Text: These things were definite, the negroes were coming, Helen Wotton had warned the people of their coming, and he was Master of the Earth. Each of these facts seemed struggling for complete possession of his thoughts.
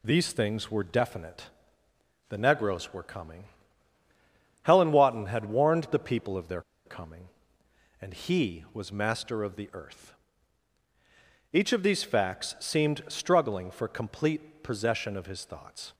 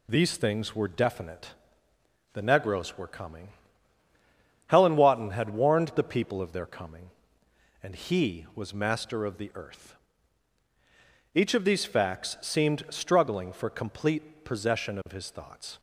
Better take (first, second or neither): second